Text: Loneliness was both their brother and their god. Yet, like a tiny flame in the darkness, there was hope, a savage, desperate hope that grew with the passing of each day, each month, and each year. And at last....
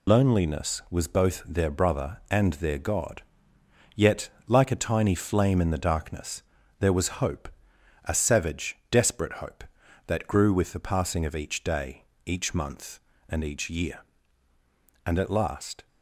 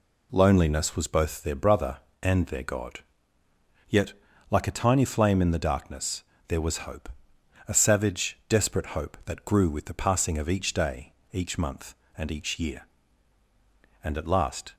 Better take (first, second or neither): second